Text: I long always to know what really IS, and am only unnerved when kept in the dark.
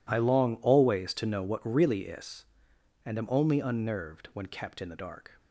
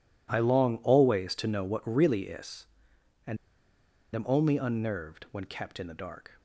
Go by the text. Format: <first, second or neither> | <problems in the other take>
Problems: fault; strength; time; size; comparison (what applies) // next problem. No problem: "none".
first | pauses between "and" and "am"; noticeable; at 3.3 s; 0.78 s long